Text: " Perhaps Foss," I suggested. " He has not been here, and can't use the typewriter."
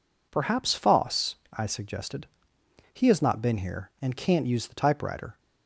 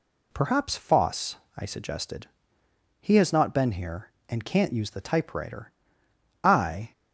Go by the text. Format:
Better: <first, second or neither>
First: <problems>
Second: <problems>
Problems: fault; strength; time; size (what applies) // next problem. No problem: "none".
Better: first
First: none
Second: goes on to say "I"; from 6.4 s on; 0.50 s long